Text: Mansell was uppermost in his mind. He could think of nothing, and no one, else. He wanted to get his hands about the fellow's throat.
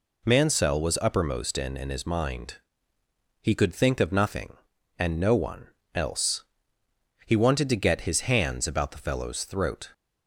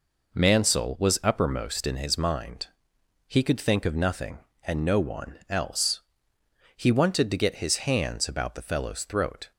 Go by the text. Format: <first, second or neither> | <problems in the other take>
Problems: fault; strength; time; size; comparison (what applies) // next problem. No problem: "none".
second | says "in" twice; at 1.7 s